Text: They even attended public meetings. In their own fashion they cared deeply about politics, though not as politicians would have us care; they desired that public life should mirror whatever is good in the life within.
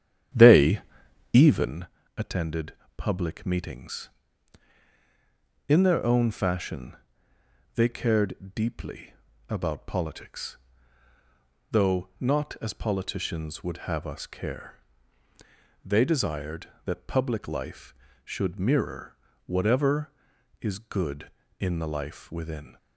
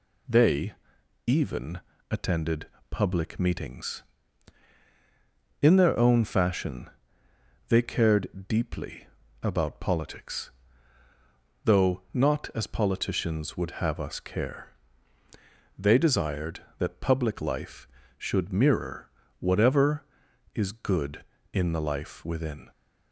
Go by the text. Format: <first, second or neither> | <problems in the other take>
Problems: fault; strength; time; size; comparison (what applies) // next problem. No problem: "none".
second | starts louder than the rest; strong; until 1.8 s; 10 dB // pauses between "They" and "even"; noticeable; at 0.7 s; 0.54 s long; noticeable in the second // pauses between "even" and "attended"; slight; at 1.8 s; 0.30 s long; slight in the second // pauses between "attended" and "public"; slight; at 2.7 s; 0.24 s long; slight in the second // pauses between "fashion" and "they"; noticeable; at 6.9 s; 0.80 s long; noticeable in the second // pauses between "deeply" and "about"; slight; at 9.1 s; 0.36 s long; slight in the second // pauses between "mirror" and "whatever"; slight; at 19.1 s; 0.30 s long; slight in the second